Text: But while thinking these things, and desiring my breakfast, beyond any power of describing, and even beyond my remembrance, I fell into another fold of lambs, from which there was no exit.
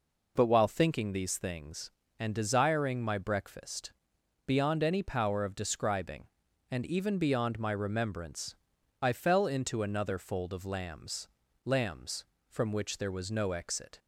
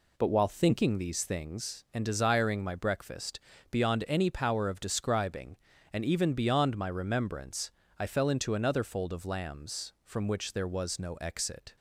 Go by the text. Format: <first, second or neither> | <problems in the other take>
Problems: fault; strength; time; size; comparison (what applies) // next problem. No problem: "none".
second | says "lambs" twice; at 11.6 s